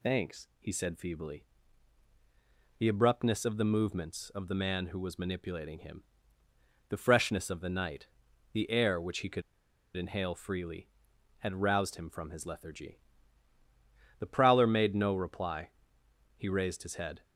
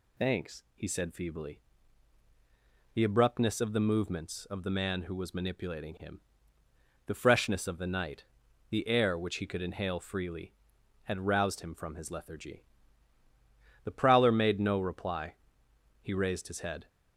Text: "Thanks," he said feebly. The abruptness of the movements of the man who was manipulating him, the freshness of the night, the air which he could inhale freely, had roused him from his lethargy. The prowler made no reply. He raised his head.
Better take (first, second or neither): second